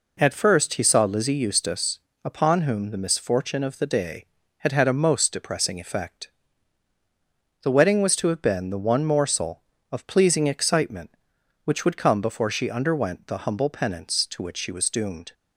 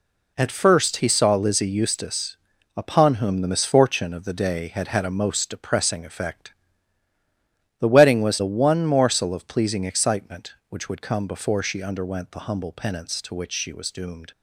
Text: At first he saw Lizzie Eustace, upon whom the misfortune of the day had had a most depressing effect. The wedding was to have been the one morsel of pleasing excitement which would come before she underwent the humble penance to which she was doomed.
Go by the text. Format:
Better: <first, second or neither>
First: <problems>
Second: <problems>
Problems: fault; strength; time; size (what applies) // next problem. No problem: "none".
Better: first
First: none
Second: skips "to have been"; at 8.3 s